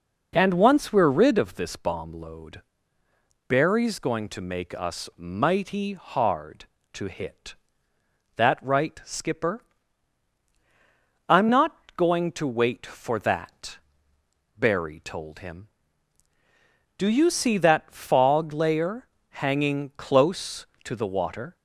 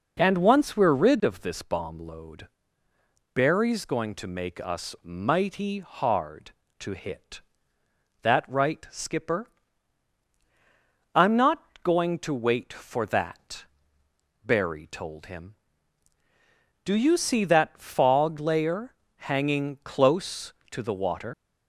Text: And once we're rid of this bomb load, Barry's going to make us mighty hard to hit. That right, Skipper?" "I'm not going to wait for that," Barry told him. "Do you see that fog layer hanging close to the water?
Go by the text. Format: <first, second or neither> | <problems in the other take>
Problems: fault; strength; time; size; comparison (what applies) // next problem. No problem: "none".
first | pauses between "not" and "going"; slight; at 11.6 s; 0.20 s long; slight in the first // pauses between "layer" and "hanging"; slight; at 18.9 s; 0.28 s long; slight in the first // leaves "water" unfinished; at 21.3 s; 85 ms